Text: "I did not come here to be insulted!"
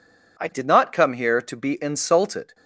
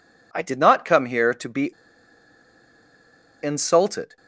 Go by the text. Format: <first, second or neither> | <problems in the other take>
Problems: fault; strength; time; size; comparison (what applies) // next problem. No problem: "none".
first | pauses between "be" and "insulted"; strong; at 1.7 s; 1.6 s long